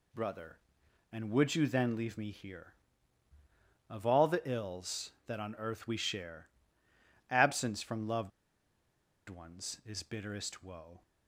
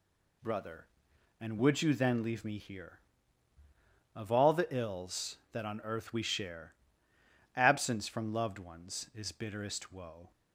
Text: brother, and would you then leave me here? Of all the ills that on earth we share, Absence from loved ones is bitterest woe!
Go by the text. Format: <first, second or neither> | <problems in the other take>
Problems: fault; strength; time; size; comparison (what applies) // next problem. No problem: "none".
second | pauses between "loved" and "ones"; at 8.3 s; 0.99 s long